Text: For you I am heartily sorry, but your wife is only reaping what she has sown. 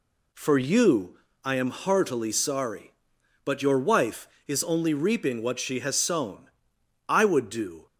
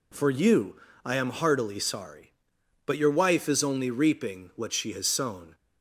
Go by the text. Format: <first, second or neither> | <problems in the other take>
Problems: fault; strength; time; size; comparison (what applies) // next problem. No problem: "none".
second | pauses between "you" and "I"; slight; at 1.1 s; 0.26 s long; slight in the second // goes on to say "I would do"; noticeable; from 7.0 s on; 0.78 s long